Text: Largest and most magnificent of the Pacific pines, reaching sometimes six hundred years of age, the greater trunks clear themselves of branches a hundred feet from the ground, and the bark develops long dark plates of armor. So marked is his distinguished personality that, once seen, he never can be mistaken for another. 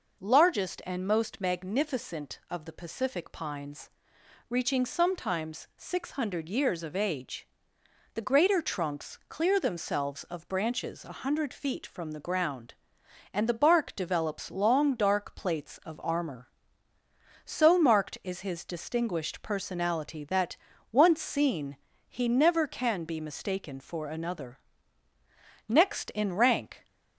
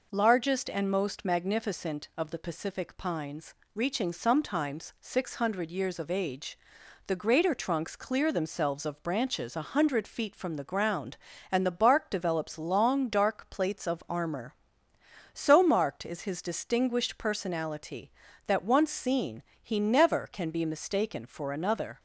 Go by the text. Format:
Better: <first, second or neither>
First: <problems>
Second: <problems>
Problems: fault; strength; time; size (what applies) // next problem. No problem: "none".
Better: second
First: goes on to say "Next in rank"; noticeable; from 25.6 s on; 1.1 s long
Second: none